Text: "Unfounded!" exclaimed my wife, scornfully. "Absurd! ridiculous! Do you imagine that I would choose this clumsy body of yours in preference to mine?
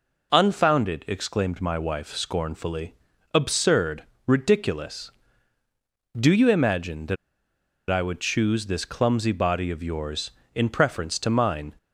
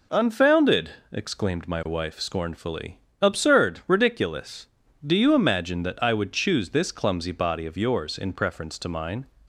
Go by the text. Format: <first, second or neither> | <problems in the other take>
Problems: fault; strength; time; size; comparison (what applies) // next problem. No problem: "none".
second | pauses between "that" and "I"; noticeable; at 7.1 s; 0.75 s long